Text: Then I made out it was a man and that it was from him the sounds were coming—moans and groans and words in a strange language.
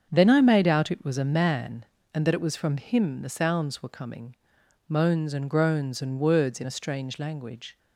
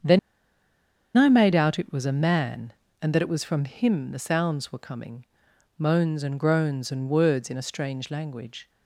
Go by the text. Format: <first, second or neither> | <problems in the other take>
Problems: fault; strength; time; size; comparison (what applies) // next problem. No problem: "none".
first | starts louder than the rest; until 2.0 s; 7 dB; strong in the first // pauses between "Then" and "I"; at 0.1 s; 0.98 s long